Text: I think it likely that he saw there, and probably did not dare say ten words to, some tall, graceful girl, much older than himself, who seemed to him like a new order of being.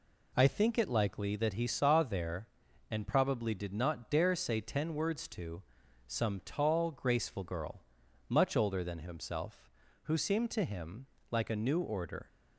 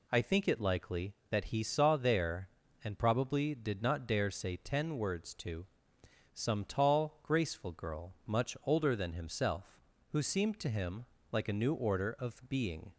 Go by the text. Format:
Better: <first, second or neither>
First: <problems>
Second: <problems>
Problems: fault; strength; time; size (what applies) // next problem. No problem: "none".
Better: second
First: pauses between "him" and "like"; slight; at 11.0 s; 0.24 s long // stops before "of being"; at 12.2 s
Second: pauses between "him" and "like"; slight; at 11.0 s; 0.28 s long